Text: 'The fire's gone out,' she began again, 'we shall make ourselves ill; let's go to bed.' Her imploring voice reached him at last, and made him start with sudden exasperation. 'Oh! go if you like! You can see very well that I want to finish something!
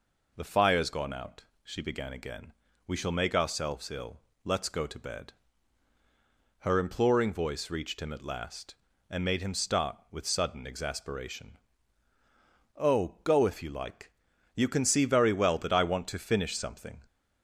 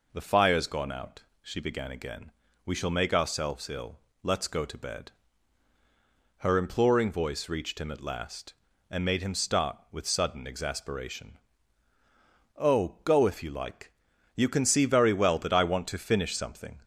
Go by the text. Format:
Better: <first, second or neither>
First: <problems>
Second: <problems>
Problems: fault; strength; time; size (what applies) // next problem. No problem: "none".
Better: neither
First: none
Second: none